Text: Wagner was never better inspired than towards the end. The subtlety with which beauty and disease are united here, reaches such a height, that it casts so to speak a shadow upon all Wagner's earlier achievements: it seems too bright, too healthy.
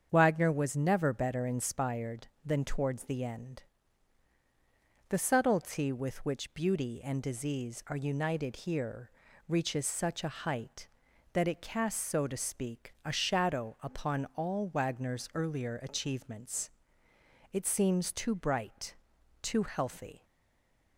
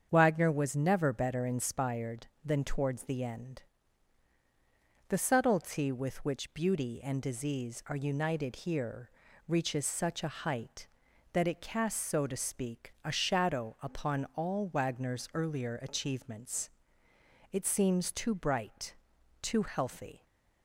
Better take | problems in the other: second | starts louder than the rest; strong; until 1.1 s; 7.5 dB; strong in the second // stays silent after the last word; slight; from 20.2 s on; 0.7 s long

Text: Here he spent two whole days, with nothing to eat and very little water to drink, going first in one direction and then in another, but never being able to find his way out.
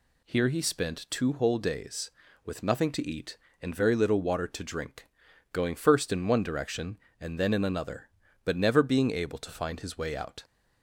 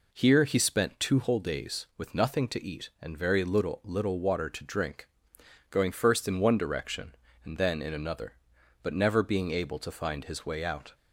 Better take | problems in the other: first | says "little" twice; at 3.8 s

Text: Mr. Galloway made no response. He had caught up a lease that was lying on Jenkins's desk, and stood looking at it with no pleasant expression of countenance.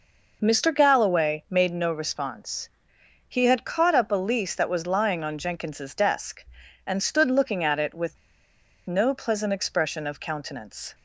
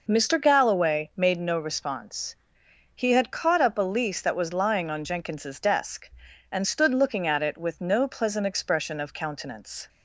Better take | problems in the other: second | pauses between "with" and "no"; noticeable; at 8.1 s; 0.70 s long

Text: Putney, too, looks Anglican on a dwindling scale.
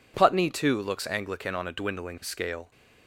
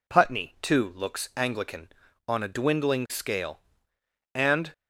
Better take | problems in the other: first | goes on to say "And"; slight; from 4.3 s on; 0.38 s long

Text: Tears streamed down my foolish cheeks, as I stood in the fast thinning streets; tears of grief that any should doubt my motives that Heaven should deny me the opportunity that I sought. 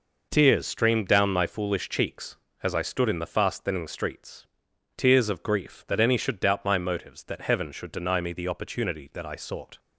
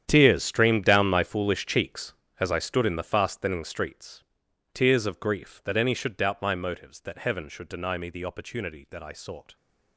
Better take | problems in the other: first | gets quieter; strong; throughout; 15 dB

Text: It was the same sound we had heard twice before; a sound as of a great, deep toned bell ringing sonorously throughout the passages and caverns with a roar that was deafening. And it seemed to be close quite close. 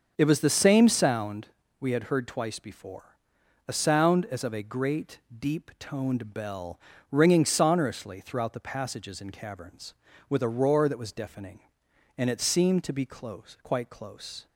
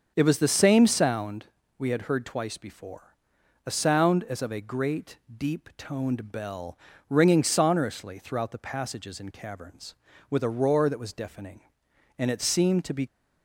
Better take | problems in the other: first | starts louder than the rest; until 1.1 s; 6.5 dB; also in the first // pauses between "sound" and "we"; slight; at 1.4 s; 0.34 s long; slight in the first // pauses between "bell" and "ringing"; slight; at 6.7 s; 0.32 s long; slight in the first // stops before "close quite close"; at 13.0 s

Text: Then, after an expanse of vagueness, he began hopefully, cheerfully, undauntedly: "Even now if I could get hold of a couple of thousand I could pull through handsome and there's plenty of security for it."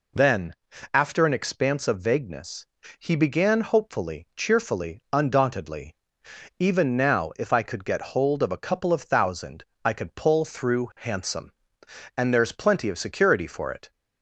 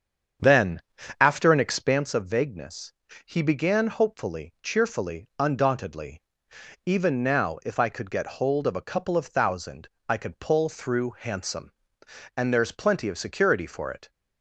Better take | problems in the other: first | starts louder than the rest; strong; until 2.1 s; 7.5 dB // pauses between "thousand" and "I"; slight; at 9.8 s; 0.20 s long; slight in the first

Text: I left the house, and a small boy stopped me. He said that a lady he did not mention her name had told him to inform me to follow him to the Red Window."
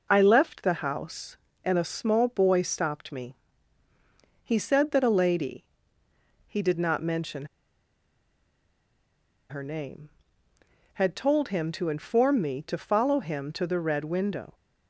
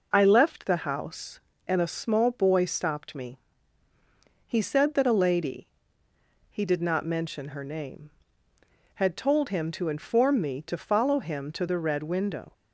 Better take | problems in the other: second | pauses between "lady" and "he"; noticeable; at 5.6 s; 0.86 s long; noticeable in the second // pauses between "mention" and "her"; strong; at 7.4 s; 2.0 s long

